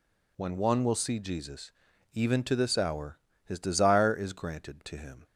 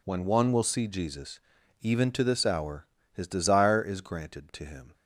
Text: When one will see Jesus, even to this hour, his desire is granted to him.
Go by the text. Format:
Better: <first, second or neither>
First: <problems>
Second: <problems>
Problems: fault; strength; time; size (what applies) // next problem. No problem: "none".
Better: first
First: none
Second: gets quieter; strong; throughout; 12.5 dB